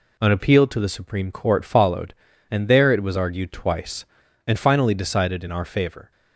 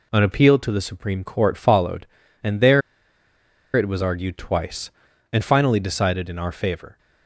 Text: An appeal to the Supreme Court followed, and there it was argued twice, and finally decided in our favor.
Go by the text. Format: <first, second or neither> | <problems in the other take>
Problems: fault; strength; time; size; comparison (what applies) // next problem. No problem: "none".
first | pauses between "there" and "it"; noticeable; at 2.8 s; 0.94 s long